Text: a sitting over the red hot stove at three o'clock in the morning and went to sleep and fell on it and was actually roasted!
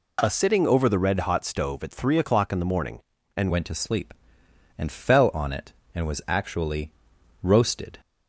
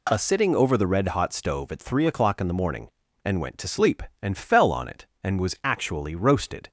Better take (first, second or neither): second